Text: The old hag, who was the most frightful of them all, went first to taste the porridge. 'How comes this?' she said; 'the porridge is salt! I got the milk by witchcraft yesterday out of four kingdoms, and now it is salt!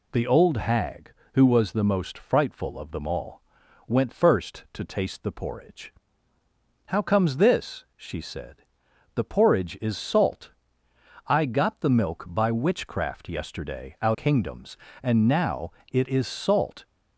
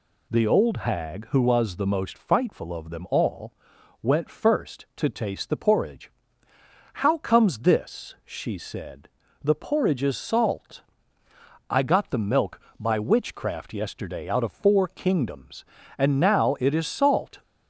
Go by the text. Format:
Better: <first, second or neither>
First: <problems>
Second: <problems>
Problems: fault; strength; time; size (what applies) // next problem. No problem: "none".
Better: second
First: skips "of four"; at 14.1 s // pauses between "now" and "it"; slight; at 15.7 s; 0.22 s long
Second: none